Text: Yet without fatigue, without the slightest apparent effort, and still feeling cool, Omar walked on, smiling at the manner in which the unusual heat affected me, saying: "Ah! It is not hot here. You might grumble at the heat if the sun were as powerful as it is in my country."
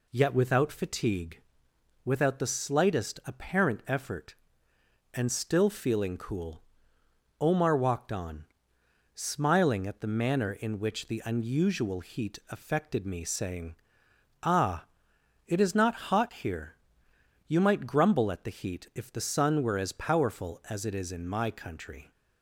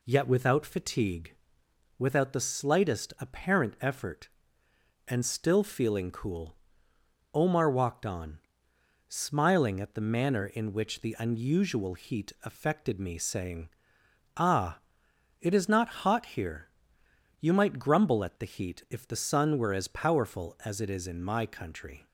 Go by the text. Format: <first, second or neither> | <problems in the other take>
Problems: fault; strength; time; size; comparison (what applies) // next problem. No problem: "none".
neither | none